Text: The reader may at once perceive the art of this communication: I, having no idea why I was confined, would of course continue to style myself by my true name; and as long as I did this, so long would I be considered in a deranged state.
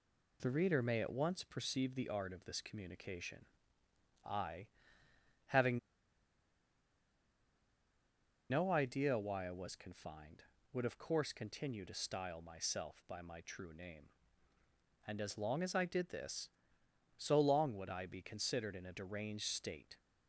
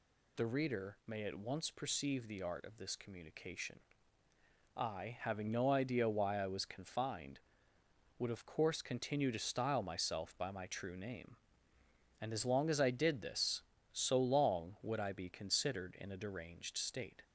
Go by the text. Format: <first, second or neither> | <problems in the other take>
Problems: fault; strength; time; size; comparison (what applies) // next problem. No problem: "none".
second | pauses between "having" and "no"; strong; at 5.7 s; 2.7 s long